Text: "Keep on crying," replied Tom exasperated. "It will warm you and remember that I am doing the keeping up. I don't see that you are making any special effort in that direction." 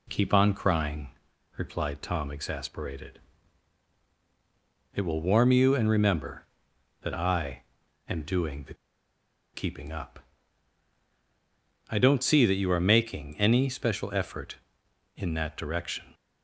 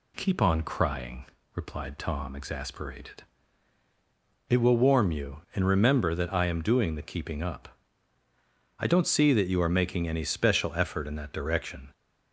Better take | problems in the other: second | pauses between "I" and "am"; noticeable; at 7.6 s; 0.46 s long // pauses between "the" and "keeping"; noticeable; at 8.7 s; 0.79 s long

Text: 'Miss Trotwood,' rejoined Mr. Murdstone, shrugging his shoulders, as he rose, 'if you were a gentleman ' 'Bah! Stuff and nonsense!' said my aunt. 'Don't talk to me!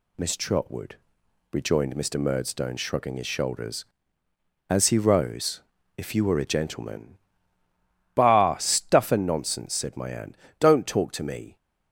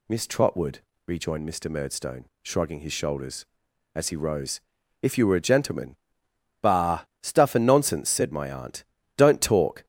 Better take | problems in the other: first | stops before "to me"; at 9.8 s

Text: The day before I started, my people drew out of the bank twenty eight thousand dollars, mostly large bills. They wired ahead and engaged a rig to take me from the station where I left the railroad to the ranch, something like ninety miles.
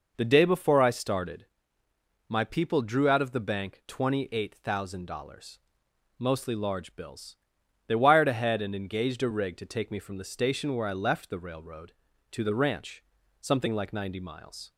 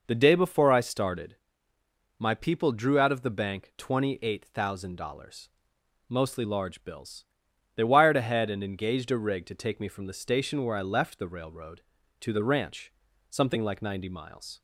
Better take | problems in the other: neither | none

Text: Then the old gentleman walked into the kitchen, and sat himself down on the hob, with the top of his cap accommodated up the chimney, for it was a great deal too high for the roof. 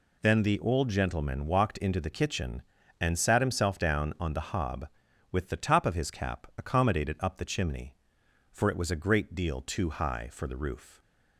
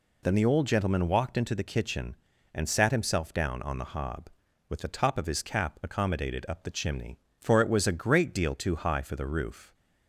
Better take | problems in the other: neither | none

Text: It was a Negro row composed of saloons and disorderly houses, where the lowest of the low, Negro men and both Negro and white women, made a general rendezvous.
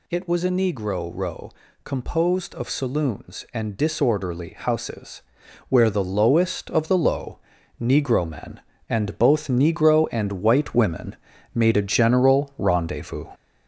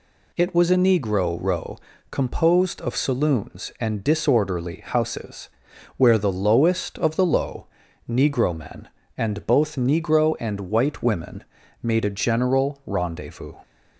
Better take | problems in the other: second | gets louder; noticeable; throughout; 5 dB // pauses between "row" and "composed"; slight; at 1.4 s; 0.34 s long; slight in the second

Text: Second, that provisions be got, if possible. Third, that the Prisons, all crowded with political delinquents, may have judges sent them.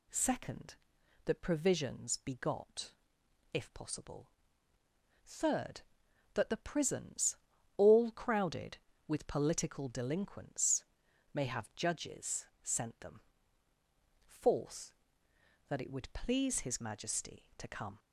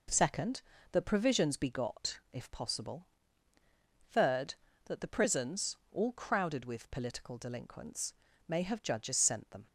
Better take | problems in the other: second | pauses between "judges" and "sent"; slight; at 12.4 s; 0.16 s long // goes on to say "Fourth that it would please his Majesty to come"; strong; from 14.2 s on; 3.7 s long

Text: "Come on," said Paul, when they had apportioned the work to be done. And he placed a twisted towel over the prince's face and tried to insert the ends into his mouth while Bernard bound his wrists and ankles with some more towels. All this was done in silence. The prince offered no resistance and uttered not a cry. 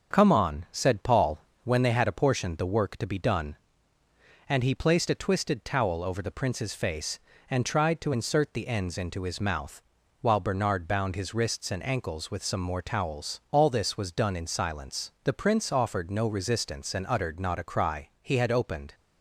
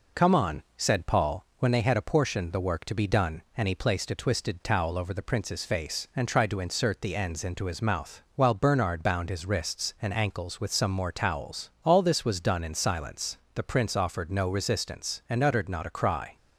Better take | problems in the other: second | starts louder than the rest; until 1.1 s; 6.5 dB // pauses between "mouth" and "while"; at 9.8 s; 0.40 s long // goes on to say "He had opened"; noticeable; from 18.2 s on; 0.74 s long

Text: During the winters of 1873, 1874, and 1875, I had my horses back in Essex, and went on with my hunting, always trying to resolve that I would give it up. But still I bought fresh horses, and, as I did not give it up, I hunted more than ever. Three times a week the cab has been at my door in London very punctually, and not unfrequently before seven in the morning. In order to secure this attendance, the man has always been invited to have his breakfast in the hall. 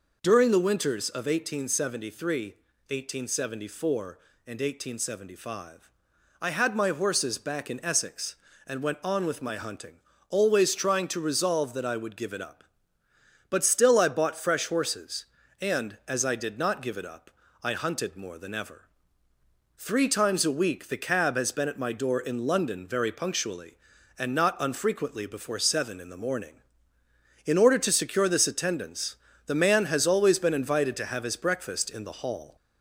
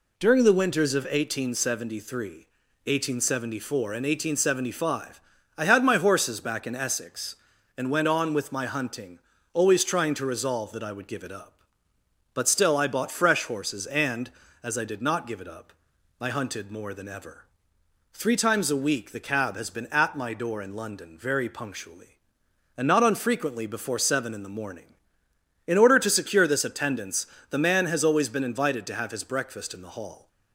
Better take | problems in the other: second | gets louder; slight; throughout; 2.5 dB

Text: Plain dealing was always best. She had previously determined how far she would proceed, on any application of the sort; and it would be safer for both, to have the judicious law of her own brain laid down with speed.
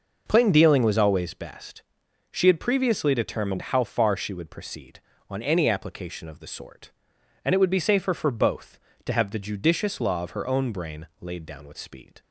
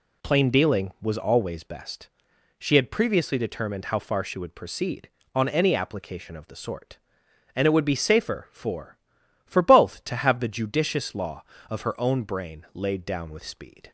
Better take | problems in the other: first | says "for" twice; at 9.4 s

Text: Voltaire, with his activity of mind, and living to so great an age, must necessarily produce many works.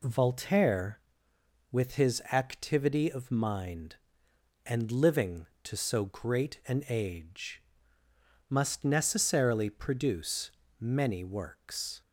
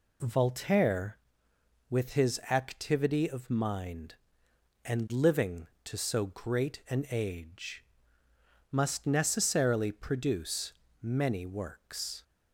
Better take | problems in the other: neither | pauses between "produce" and "many"; slight; the same in both

